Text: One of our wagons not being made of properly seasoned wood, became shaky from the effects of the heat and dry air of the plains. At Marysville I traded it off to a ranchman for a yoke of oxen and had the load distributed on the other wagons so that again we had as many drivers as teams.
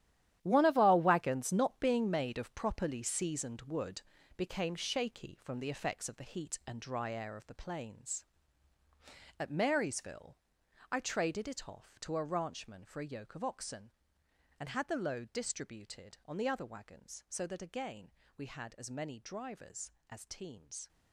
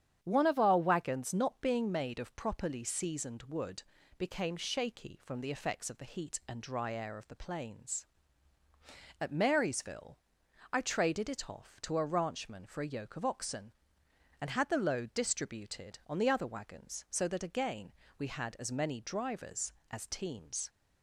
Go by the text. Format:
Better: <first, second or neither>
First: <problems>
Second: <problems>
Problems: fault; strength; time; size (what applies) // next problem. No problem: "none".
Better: second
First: gets quieter; strong; throughout; 12 dB // starts louder than the rest; strong; until 1.4 s; 11.5 dB // pauses between "Marysville" and "I"; noticeable; at 10.3 s; 0.52 s long // pauses between "again" and "we"; slight; at 18.0 s; 0.28 s long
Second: starts louder than the rest; strong; until 1.2 s; 9 dB // pauses between "Marysville" and "I"; noticeable; at 10.1 s; 0.52 s long // pauses between "again" and "we"; slight; at 17.9 s; 0.28 s long